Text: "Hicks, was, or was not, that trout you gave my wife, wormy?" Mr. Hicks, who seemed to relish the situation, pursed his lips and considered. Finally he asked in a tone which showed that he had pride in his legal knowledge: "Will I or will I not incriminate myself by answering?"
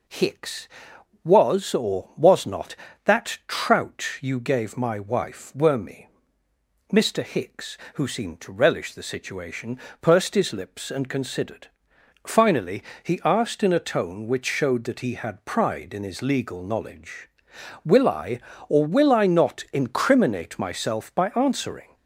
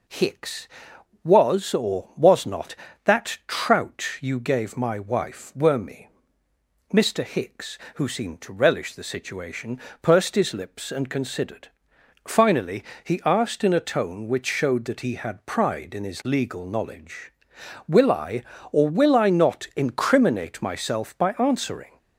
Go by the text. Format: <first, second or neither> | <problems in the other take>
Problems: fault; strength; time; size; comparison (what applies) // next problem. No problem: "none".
neither | pauses between "Finally" and "he"; slight; the same in both